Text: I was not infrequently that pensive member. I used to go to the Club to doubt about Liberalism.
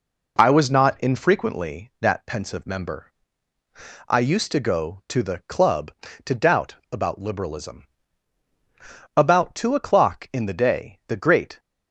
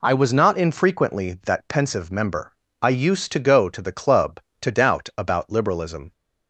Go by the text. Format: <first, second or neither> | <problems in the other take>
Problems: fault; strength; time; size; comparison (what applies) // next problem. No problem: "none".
second | pauses between "doubt" and "about"; slight; at 6.7 s; 0.16 s long // goes on to say "About two o'clock in the day the great"; strong; from 9.1 s on; 2.4 s long